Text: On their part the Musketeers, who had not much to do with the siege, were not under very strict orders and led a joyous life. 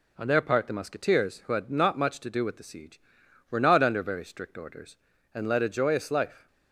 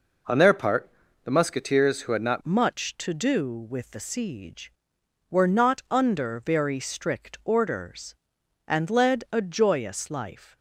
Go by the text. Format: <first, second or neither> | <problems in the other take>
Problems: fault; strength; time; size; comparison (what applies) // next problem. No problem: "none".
first | pauses between "part" and "the"; slight; at 0.8 s; 0.36 s long // changes voice at "much"; from 2.4 s on; 8.1 s long